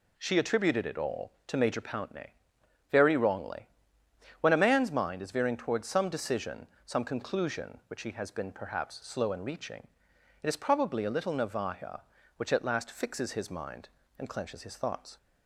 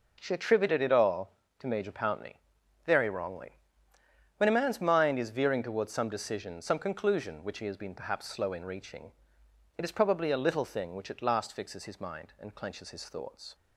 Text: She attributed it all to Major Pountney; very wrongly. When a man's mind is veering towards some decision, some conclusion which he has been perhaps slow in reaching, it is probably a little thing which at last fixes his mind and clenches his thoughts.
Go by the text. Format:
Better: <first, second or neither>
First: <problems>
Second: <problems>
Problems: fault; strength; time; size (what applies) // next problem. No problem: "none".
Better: second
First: says "navaja" for "thing"; at 11.3 s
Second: none